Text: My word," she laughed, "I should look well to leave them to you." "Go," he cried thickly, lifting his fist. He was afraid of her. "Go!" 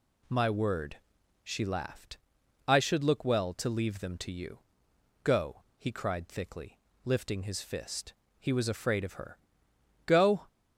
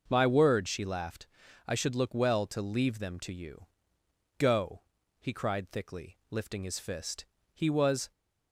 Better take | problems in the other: first | stops before "afraid of her Go"; at 8.1 s

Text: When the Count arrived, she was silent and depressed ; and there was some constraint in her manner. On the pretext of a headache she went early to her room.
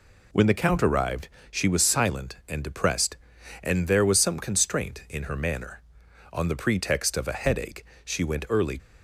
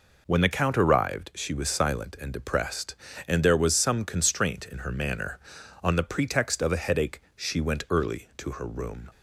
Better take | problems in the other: second | pauses between "headache" and "she"; slight; at 7.8 s; 0.22 s long; slight in the second // stops before "to her room"; at 8.7 s

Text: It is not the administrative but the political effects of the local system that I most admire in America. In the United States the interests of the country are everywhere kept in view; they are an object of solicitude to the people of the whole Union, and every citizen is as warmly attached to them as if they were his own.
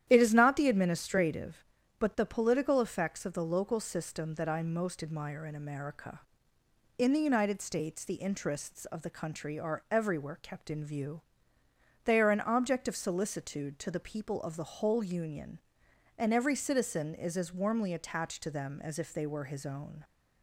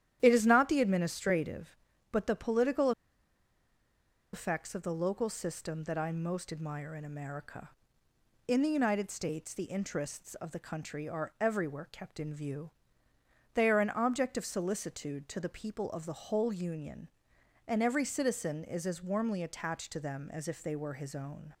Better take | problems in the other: first | starts louder than the rest; strong; until 1.2 s; 11 dB; strong in the first // pauses between "political" and "effects"; strong; at 2.9 s; 1.4 s long

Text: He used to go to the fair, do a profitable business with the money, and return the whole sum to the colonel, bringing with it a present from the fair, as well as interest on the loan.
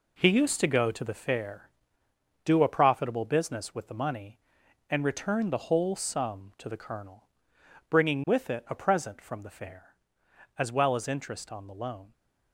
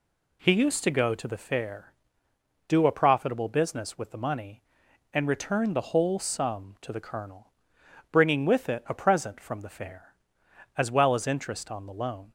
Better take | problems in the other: second | gets quieter; strong; throughout; 8 dB

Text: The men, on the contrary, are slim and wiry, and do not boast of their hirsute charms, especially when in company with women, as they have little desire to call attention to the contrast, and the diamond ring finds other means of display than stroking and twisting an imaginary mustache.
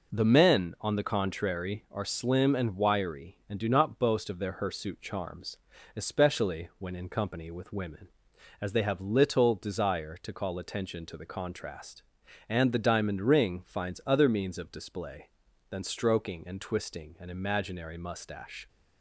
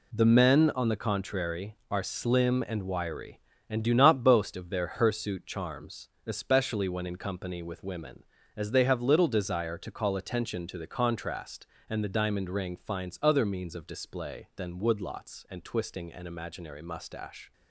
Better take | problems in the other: first | says "woodlots" for "stroking"; at 14.8 s

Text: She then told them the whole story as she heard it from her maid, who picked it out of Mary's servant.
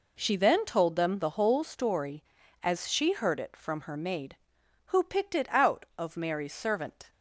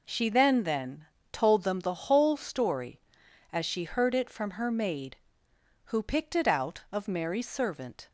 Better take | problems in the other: first | says "then" twice; at 0.6 s

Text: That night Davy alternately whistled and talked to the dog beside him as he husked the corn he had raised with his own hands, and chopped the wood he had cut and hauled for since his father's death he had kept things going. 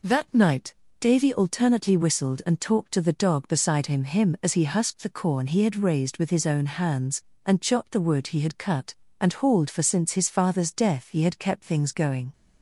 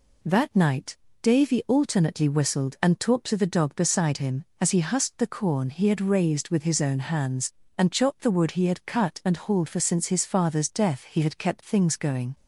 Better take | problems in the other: second | pauses between "night" and "Davy"; slight; at 0.7 s; 0.24 s long; slight in the second // says "him" twice; at 4.0 s

